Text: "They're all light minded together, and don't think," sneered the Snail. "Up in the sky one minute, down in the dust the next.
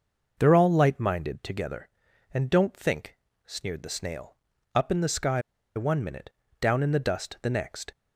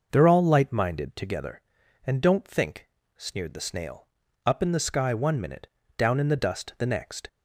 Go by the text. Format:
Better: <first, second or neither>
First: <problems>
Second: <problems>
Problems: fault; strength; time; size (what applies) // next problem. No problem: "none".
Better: second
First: pauses between "sky" and "one"; slight; at 5.4 s; 0.34 s long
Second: none